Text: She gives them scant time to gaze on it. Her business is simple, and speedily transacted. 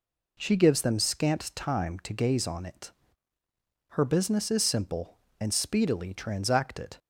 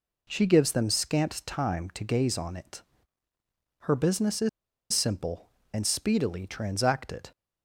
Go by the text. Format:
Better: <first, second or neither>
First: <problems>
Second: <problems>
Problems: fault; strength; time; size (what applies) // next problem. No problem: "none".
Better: first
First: none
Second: pauses between "is" and "simple"; at 4.4 s; 0.43 s long